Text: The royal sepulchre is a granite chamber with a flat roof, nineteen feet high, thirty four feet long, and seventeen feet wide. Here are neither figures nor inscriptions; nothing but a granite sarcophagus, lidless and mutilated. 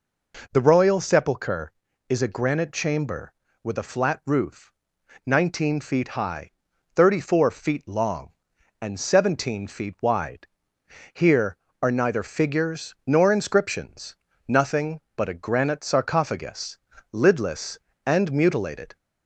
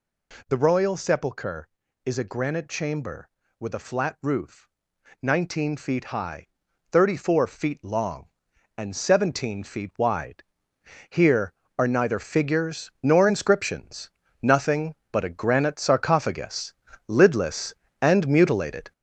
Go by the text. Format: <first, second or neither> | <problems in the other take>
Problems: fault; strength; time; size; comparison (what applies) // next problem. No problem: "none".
first | gets louder; noticeable; throughout; 4.5 dB